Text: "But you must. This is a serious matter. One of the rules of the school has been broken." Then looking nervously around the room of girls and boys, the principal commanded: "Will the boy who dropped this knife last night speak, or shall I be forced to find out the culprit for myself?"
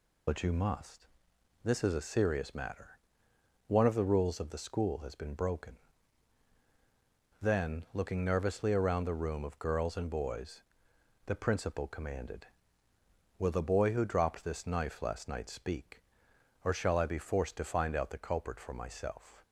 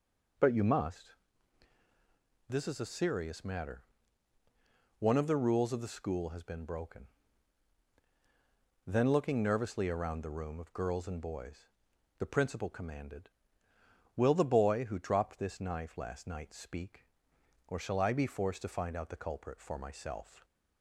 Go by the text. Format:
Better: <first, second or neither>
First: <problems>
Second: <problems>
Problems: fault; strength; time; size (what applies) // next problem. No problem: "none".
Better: second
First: loses the start of "But"; at 0.2 s; 55 ms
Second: none